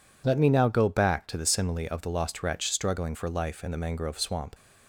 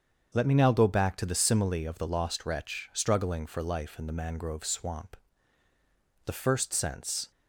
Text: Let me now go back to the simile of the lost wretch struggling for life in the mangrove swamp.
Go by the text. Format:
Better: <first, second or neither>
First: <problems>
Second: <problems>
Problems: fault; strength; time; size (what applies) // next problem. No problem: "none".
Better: first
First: none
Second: starts louder than the rest; until 1.3 s; 7 dB // goes on to say "The first sense"; noticeable; from 6.2 s on; 1.0 s long